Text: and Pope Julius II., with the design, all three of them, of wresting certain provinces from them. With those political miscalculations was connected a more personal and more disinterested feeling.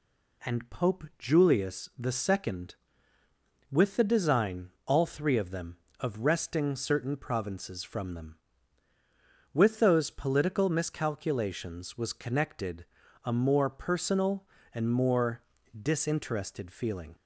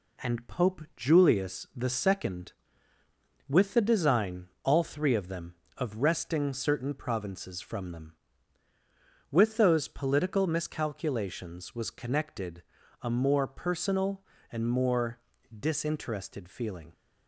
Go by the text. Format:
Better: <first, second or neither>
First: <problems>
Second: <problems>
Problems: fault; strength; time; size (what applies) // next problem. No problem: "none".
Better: first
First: pauses between "connected" and "a"; at 12.8 s; 0.38 s long // pauses between "more" and "disinterested"; at 15.4 s; 0.38 s long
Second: gets quieter; slight; throughout; 3 dB // pauses between "connected" and "a"; at 12.6 s; 0.38 s long // pauses between "more" and "disinterested"; at 15.1 s; 0.38 s long